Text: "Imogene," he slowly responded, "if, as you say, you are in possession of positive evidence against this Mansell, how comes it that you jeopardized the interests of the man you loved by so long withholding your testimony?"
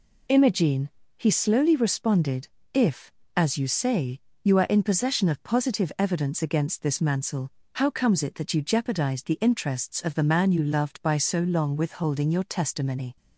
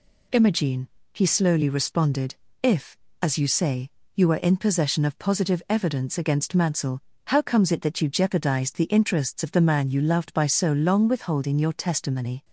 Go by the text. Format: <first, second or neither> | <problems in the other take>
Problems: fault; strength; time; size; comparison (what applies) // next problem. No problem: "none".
first | skips "this"; at 6.5 s